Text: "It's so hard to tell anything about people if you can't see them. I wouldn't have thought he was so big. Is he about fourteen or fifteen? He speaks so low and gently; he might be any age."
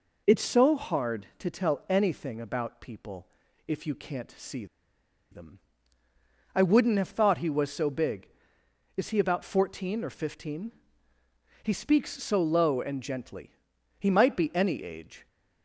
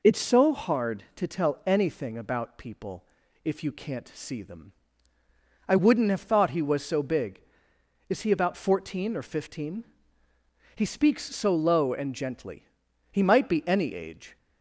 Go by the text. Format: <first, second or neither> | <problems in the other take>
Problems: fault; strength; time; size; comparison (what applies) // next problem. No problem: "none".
second | pauses between "people" and "if"; at 3.2 s; 0.40 s long; also in the second // pauses between "see" and "them"; noticeable; at 4.6 s; 0.66 s long